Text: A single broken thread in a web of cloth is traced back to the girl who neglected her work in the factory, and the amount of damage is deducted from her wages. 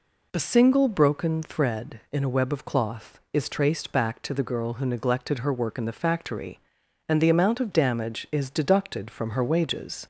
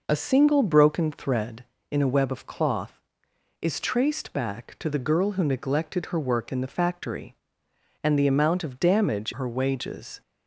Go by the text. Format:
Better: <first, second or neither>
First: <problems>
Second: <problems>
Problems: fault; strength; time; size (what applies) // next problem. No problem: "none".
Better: first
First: none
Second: skips "is deducted from"; at 9.3 s